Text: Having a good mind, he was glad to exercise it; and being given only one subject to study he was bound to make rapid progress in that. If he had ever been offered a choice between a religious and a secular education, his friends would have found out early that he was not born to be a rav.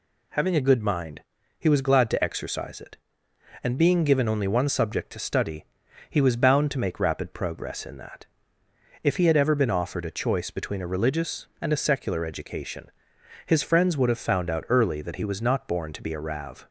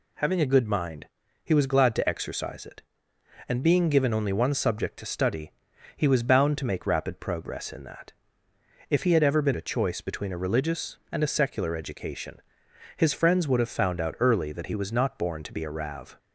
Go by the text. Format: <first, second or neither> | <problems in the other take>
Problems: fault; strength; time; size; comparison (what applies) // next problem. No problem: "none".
first | pauses between "study" and "he"; at 5.5 s; 0.44 s long; also in the first // skips "offered"; at 9.5 s